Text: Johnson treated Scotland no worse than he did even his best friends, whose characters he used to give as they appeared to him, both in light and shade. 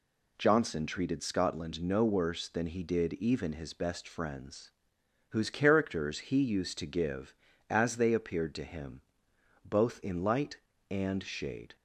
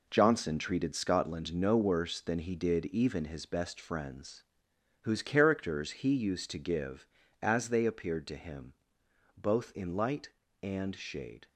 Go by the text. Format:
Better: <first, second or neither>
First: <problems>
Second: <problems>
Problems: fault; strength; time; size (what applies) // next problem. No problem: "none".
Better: first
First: none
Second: gets quieter; strong; throughout; 8 dB